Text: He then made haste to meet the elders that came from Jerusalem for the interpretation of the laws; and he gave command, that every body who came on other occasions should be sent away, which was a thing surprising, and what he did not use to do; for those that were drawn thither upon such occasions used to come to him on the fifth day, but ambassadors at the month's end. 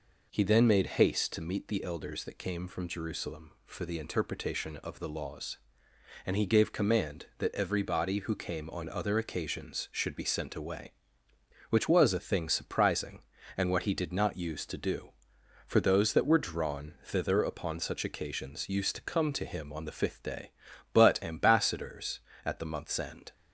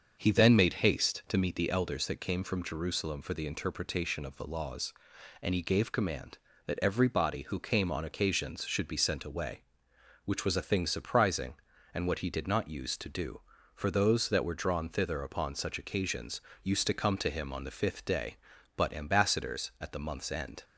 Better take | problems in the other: first | starts louder than the rest; until 1.2 s; 6.5 dB // skips "other"; at 8.0 s // pauses between "occasions" and "used"; slight; at 16.4 s; 0.22 s long

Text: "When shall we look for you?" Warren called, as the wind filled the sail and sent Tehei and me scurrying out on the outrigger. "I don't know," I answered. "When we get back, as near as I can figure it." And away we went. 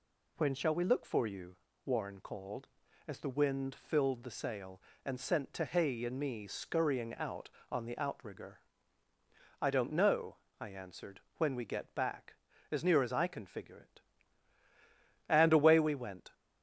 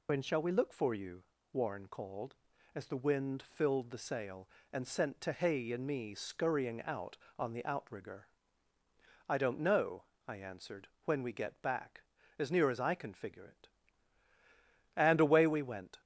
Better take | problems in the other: first | loses the start of "When"; at 0.0 s; 50 ms

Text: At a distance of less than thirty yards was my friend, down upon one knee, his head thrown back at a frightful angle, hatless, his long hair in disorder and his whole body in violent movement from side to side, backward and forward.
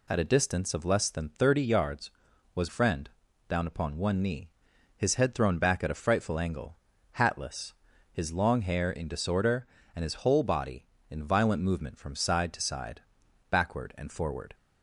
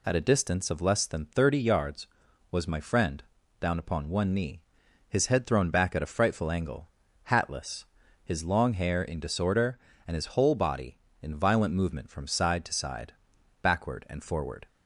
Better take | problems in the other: second | skips "my"; at 2.6 s

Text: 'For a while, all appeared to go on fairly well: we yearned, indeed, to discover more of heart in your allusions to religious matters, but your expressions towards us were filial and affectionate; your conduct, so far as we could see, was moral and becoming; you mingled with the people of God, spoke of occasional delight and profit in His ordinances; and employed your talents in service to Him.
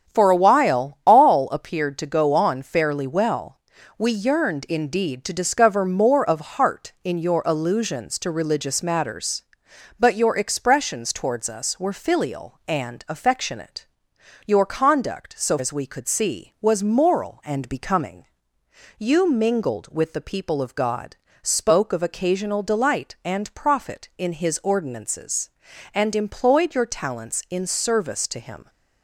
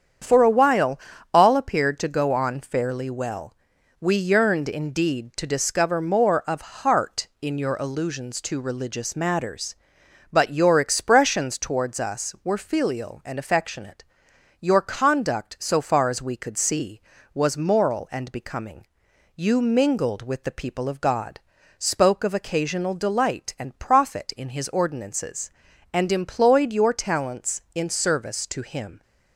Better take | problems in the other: second | starts louder than the rest; strong; until 1.1 s; 7.5 dB; strong in the second // skips "far"; at 15.5 s

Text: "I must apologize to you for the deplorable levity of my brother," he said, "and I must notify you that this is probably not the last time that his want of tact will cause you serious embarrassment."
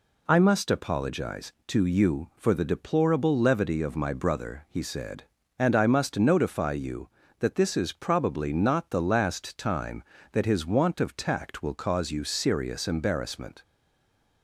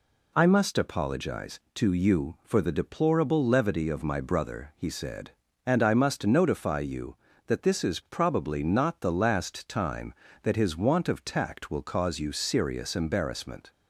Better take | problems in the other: second | stays silent after the last word; slight; from 13.6 s on; 0.8 s long

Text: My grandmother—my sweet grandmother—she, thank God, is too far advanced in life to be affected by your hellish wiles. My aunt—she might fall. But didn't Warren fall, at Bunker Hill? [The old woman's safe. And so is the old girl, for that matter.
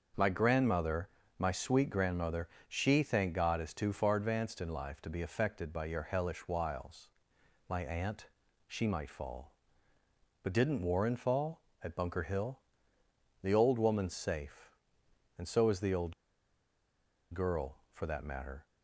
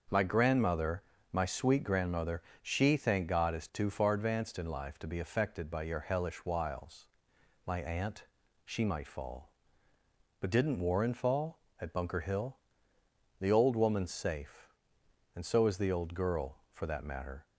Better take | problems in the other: second | starts louder than the rest; until 1.4 s; 6.5 dB; also in the second // pauses between "old" and "girl"; at 16.1 s; 1.1 s long

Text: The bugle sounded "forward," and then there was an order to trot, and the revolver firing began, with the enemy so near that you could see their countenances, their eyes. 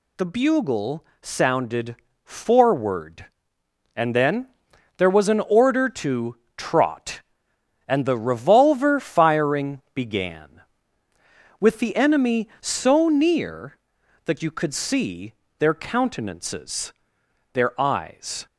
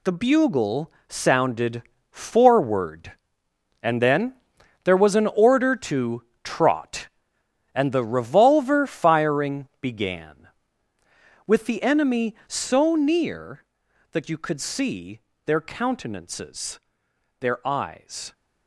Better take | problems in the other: first | gets quieter; strong; throughout; 9 dB // pauses between "bugle" and "sounded"; slight; at 0.9 s; 0.16 s long; slight in the first // pauses between "sounded" and "forward"; slight; at 1.8 s; 0.28 s long; slight in the first // pauses between "then" and "there"; noticeable; at 4.3 s; 0.48 s long; noticeable in the first // pauses between "to" and "trot"; slight; at 6.2 s; 0.20 s long; slight in the first // pauses between "see" and "their"; slight; at 15.2 s; 0.24 s long; slight in the first

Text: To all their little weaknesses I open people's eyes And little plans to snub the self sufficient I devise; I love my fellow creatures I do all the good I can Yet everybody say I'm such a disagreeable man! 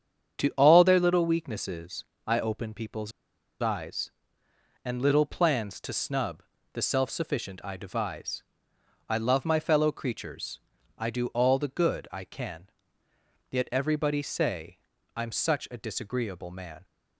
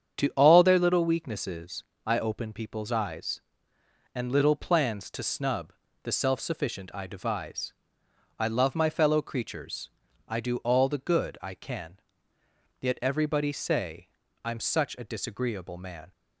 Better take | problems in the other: second | starts louder than the rest; strong; until 1.4 s; 8 dB; strong in the second // pauses between "weaknesses" and "I"; slight; at 2.0 s; 0.22 s long; slight in the second // pauses between "people's" and "eyes"; noticeable; at 3.1 s; 0.51 s long // pauses between "snub" and "the"; slight; at 6.4 s; 0.30 s long; slight in the second // pauses between "creatures" and "I"; at 10.5 s; 0.40 s long; also in the second // pauses between "can" and "Yet"; noticeable; at 12.6 s; 0.80 s long; noticeable in the second // pauses between "say" and "I'm"; slight; at 14.7 s; 0.36 s long; slight in the second

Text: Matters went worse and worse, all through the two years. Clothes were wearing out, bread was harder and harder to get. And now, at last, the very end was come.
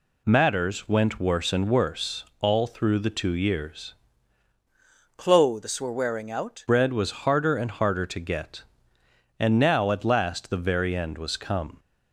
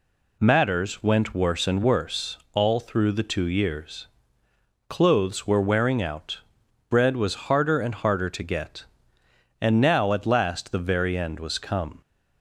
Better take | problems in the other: second | changes voice from "Clothes" to "out"; from 5.1 to 6.6 s; 1.5 s long

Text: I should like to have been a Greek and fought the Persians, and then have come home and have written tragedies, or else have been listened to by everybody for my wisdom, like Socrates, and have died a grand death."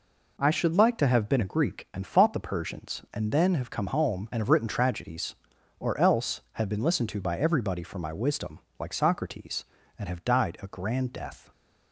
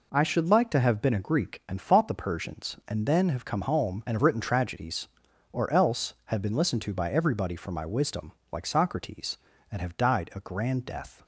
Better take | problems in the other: neither | none

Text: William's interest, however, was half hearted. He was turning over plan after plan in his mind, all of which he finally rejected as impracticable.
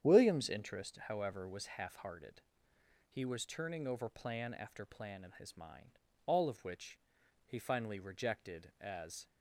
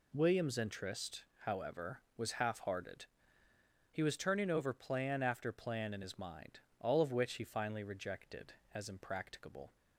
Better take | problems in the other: second | starts louder than the rest; strong; until 1.1 s; 9 dB // pauses between "which" and "he"; noticeable; at 6.9 s; 0.48 s long // stops before "impracticable"; at 9.2 s

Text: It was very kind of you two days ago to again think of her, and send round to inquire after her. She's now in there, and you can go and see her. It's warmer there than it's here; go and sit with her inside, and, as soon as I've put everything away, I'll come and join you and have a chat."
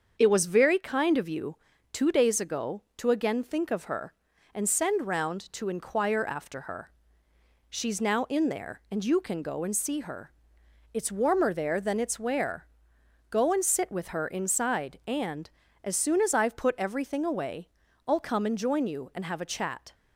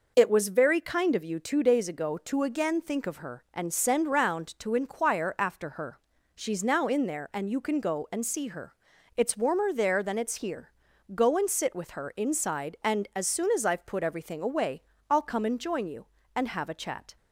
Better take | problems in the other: second | starts louder than the rest; until 1.2 s; 7 dB // pauses between "you" and "two"; slight; at 1.5 s; 0.36 s long // says "where" for "here"; at 12.1 s

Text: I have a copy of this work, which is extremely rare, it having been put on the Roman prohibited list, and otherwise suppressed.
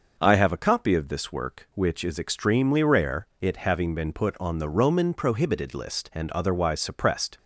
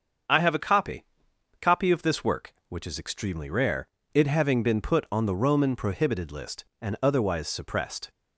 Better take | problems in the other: first | starts louder than the rest; until 1.8 s; 7 dB; noticeable in the first // says "copy" twice; at 1.5 s

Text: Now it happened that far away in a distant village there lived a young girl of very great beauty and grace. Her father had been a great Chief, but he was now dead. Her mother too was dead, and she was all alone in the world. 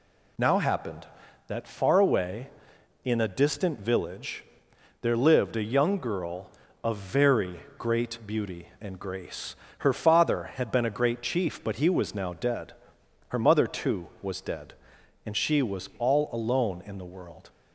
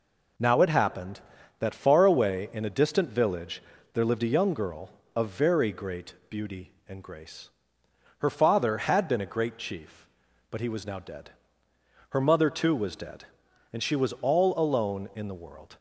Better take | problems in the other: second | skips "it"; at 0.5 s // pauses between "village" and "there"; noticeable; at 4.4 s; 0.58 s long; slight in the second // pauses between "very" and "great"; slight; at 7.5 s; 0.18 s long

